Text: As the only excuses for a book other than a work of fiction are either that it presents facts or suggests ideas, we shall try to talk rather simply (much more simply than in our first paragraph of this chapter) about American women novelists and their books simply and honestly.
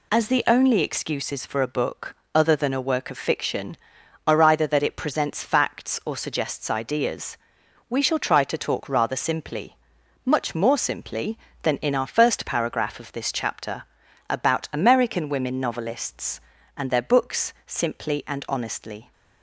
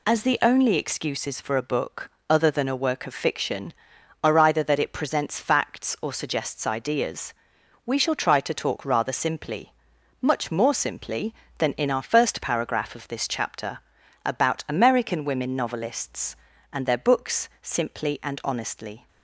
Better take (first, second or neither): neither